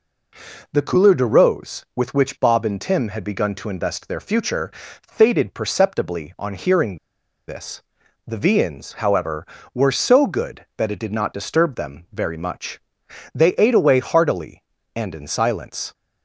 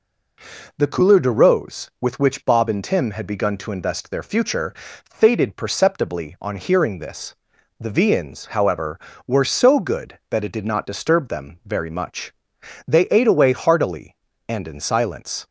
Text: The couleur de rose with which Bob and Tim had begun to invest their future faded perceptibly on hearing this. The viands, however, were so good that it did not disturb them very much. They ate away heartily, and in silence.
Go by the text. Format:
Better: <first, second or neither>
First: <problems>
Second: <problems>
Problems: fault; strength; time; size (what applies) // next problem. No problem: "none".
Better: second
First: pauses between "future" and "faded"; slight; at 4.7 s; 0.34 s long // pauses between "hearing" and "this"; noticeable; at 6.9 s; 0.52 s long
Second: pauses between "future" and "faded"; slight; at 4.7 s; 0.34 s long